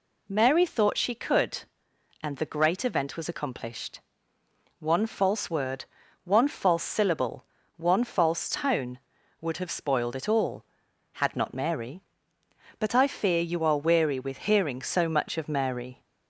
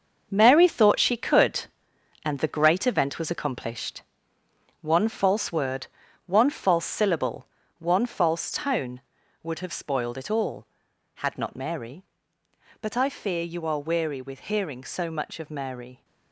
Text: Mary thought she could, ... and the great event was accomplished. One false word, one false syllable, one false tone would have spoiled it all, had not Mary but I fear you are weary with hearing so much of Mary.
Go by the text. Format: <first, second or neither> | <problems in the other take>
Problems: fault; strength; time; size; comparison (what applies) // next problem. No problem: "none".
first | gets quieter; strong; throughout; 9.5 dB